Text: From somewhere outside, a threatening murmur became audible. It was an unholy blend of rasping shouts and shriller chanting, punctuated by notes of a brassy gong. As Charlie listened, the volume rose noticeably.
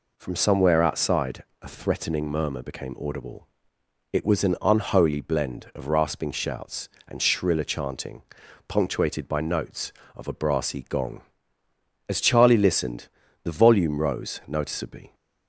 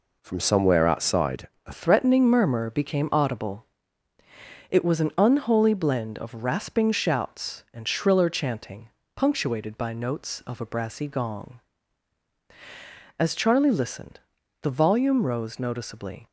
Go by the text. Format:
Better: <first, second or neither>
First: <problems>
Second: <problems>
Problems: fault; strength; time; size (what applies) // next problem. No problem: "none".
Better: first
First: none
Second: changes voice at "threatening"; from 1.7 s on; 14.5 s long